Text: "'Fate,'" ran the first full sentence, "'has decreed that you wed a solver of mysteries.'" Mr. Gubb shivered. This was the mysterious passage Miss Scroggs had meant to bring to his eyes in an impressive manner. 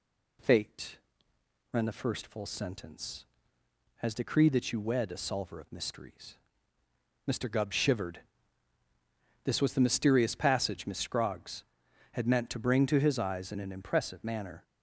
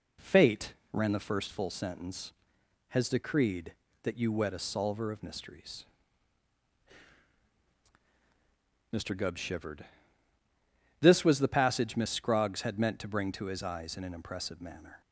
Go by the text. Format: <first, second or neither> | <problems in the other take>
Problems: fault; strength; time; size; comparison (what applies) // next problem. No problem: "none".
first | skips "mysterious"; at 11.4 s